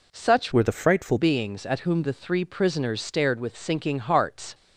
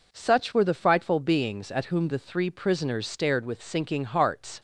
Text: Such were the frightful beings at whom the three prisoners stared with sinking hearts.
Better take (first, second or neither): second